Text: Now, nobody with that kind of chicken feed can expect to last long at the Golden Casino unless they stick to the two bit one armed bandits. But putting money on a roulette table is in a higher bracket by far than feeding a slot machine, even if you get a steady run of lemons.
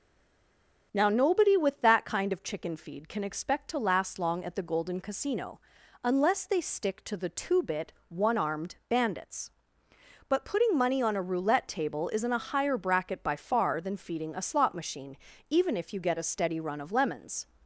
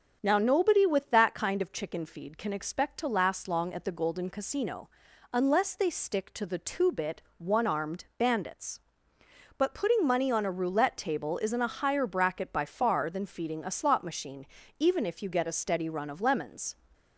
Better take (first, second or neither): second